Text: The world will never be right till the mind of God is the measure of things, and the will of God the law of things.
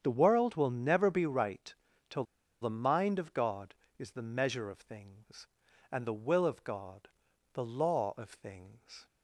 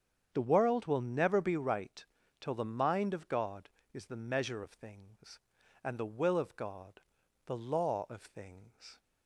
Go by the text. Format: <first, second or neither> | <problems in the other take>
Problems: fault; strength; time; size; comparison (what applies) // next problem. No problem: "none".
second | starts louder than the rest; strong; until 1.0 s; 8 dB; strong in the second // pauses between "right" and "till"; slight; at 1.7 s; 0.34 s long; slight in the second // pauses between "till" and "the"; at 2.2 s; 0.38 s long // pauses between "God" and "the"; noticeable; at 7.0 s; 0.46 s long; noticeable in the second